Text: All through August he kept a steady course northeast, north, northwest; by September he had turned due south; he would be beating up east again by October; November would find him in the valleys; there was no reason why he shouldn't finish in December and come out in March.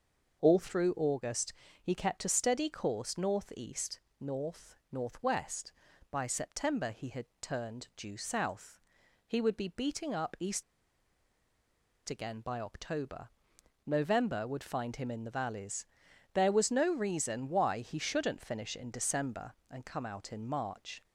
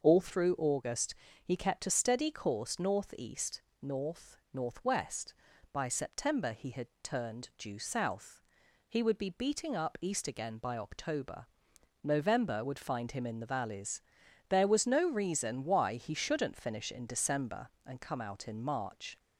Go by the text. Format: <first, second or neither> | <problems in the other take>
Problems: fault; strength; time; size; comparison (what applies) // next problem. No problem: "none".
second | starts louder than the rest; until 1.4 s; 6.5 dB; also in the second // pauses between "August" and "he"; slight; at 1.5 s; 0.30 s long; slight in the second // pauses between "had" and "turned"; slight; at 7.2 s; 0.16 s long; slight in the second // pauses between "east" and "again"; strong; at 10.6 s; 1.4 s long